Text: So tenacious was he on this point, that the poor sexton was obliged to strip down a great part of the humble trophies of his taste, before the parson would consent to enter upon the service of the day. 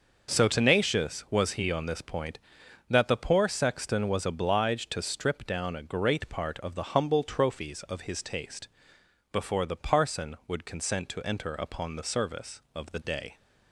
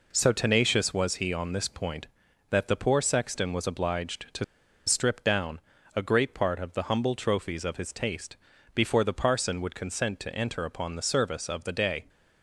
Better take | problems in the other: first | pauses between "to" and "strip"; at 4.4 s; 0.42 s long // pauses between "down" and "a"; slight; at 5.5 s; 0.36 s long

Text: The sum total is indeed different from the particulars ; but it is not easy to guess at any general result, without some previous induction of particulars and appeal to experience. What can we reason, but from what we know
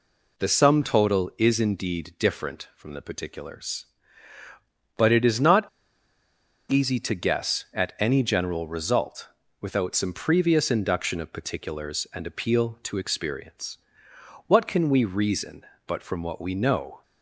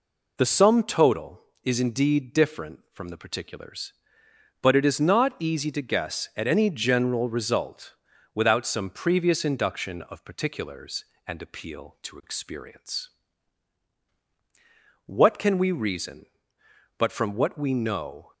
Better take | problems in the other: second | pauses between "not" and "easy"; at 5.6 s; 1.0 s long

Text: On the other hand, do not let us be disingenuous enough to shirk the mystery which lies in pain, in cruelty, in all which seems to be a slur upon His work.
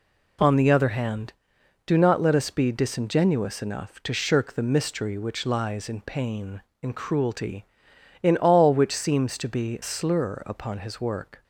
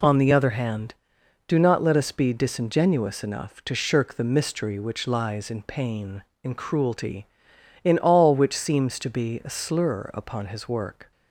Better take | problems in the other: second | skips "a"; at 9.8 s

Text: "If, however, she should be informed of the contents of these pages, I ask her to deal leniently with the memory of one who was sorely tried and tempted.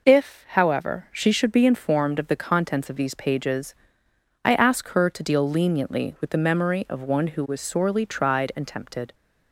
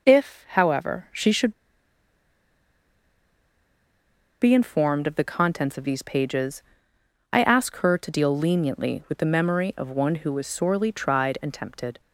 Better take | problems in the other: first | pauses between "should" and "be"; strong; at 1.5 s; 2.8 s long

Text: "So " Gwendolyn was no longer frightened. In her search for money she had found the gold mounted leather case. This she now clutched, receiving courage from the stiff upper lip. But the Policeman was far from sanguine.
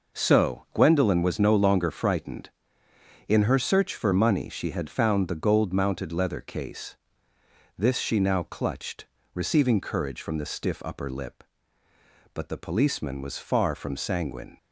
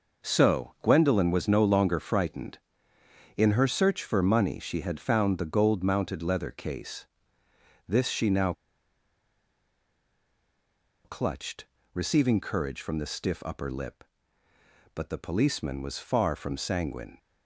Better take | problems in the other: first | pauses between "now" and "clutched"; strong; at 8.5 s; 2.5 s long

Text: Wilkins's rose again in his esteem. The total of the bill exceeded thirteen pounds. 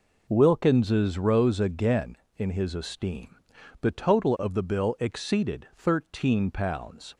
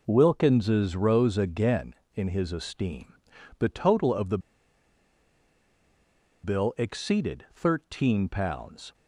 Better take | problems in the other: first | pauses between "the" and "bill"; strong; at 4.3 s; 2.0 s long

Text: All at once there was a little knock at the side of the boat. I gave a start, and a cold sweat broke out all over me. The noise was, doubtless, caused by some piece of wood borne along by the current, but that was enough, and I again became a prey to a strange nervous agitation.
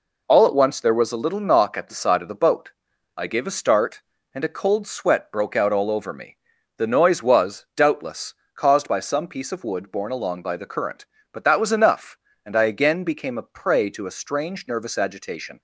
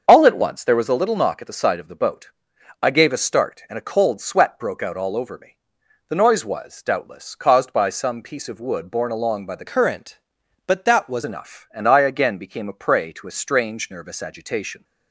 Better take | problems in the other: first | starts louder than the rest; until 1.0 s; 6.5 dB // changes voice from "current" to "was"; from 9.6 to 11.2 s; 1.6 s long

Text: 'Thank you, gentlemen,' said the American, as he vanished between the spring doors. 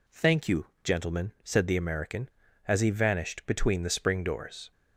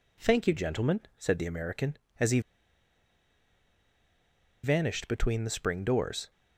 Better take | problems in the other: first | pauses between "he" and "vanished"; strong; at 2.4 s; 2.2 s long

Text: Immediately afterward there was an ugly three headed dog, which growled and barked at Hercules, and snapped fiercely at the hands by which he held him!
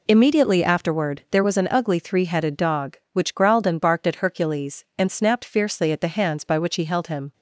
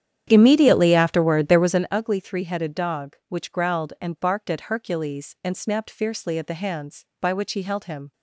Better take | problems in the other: first | starts louder than the rest; strong; until 2.0 s; 9.5 dB

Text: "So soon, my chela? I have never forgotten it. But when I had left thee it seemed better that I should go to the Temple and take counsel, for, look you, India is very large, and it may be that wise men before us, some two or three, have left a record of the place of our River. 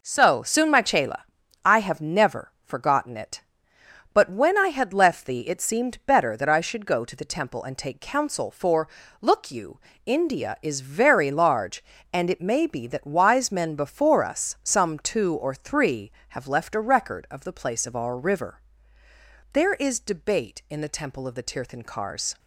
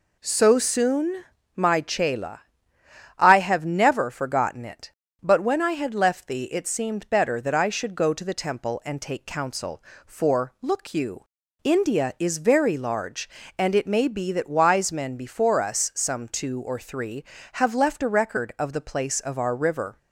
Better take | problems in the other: second | goes on to say "There is debate in the Temple of the Tirthankars"; strong; from 19.5 s on; 2.8 s long

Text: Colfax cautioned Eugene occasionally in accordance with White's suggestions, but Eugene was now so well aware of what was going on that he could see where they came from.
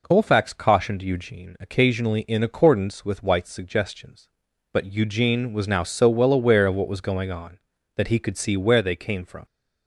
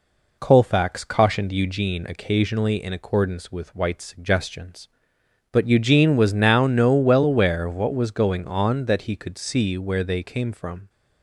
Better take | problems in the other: first | says "no" for "so"; at 6.6 s

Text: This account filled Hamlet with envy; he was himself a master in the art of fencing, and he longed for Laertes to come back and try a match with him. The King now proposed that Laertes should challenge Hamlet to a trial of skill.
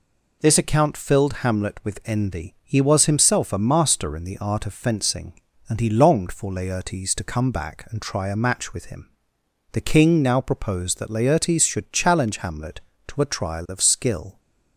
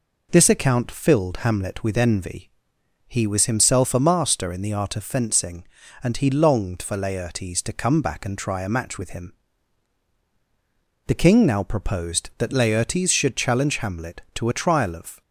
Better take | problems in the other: first | stops before "skill"; at 15.2 s

